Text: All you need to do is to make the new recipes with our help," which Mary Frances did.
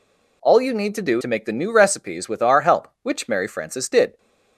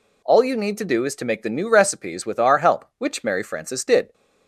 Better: second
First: skips "is"; at 1.2 s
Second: none

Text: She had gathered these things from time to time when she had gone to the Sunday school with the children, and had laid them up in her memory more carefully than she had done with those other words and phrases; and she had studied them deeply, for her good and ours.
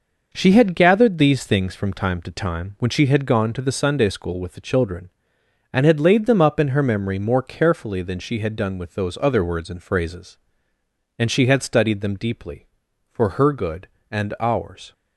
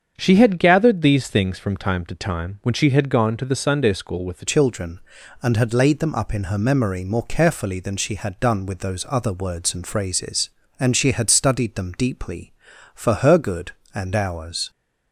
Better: first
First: none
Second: starts louder than the rest; strong; until 1.1 s; 7.5 dB // changes voice at "children"; from 4.4 s on; 10.2 s long

